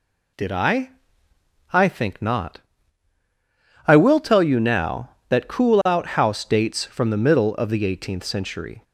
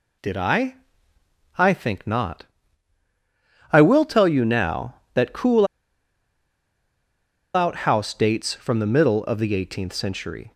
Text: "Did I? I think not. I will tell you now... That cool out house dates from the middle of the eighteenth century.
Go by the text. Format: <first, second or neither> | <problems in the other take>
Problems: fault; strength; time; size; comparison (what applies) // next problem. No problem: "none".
first | pauses between "cool" and "out"; strong; at 5.6 s; 1.8 s long